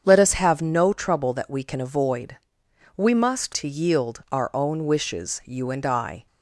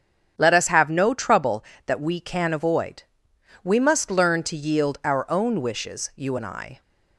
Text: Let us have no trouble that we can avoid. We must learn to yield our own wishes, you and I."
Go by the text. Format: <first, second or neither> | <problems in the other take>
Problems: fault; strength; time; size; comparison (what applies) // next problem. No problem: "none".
second | starts louder than the rest; strong; until 1.0 s; 7.5 dB; strong in the second // skips "learn"; at 3.5 s